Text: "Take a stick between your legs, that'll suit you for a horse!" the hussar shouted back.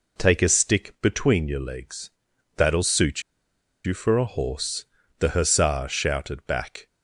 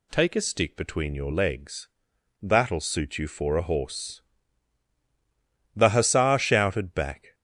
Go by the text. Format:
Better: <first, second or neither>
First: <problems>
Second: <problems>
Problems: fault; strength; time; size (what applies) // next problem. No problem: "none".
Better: second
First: pauses between "suit" and "you"; noticeable; at 3.2 s; 0.62 s long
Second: none